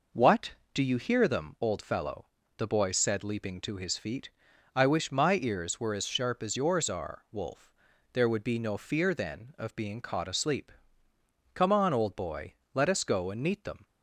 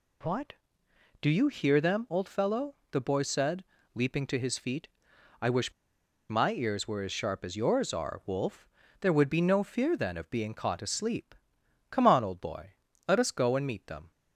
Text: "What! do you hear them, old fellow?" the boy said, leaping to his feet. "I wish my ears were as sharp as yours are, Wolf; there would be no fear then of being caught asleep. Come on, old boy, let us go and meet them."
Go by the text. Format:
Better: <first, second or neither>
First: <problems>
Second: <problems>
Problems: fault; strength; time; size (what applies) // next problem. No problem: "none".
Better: first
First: none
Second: pauses between "wish" and "my"; noticeable; at 5.7 s; 0.57 s long